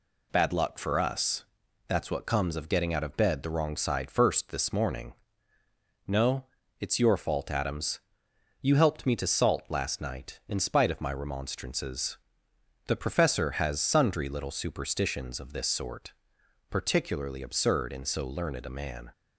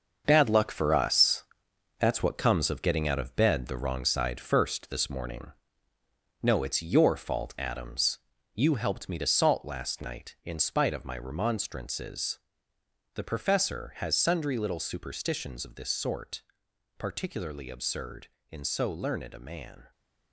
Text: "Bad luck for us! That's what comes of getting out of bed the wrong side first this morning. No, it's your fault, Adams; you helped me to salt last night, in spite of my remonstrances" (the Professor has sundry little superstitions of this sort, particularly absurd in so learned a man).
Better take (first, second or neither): first